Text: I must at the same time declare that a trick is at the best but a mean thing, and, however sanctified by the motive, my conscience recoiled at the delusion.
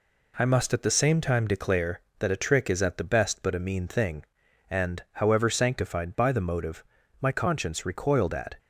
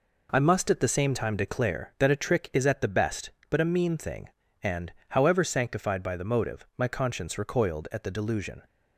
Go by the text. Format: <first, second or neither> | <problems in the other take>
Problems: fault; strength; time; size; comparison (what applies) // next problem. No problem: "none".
second | stops before "the delusion"; at 8.5 s